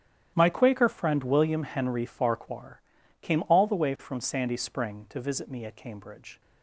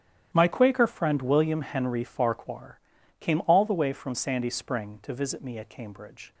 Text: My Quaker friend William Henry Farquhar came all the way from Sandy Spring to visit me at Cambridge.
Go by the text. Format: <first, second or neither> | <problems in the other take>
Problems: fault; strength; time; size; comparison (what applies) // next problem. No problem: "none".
neither | starts louder than the rest; strong; the same in both // pauses between "Farquhar" and "came"; the same in both